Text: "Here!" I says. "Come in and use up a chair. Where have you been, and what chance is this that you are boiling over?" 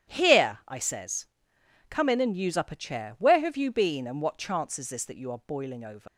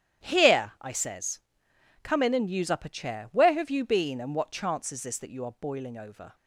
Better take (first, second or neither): second